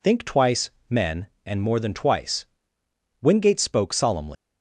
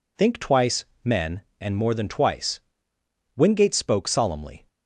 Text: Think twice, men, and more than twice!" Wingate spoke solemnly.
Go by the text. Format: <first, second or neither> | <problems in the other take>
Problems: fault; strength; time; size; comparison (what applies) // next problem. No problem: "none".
second | leaves "solemnly" unfinished; at 4.3 s; 175 ms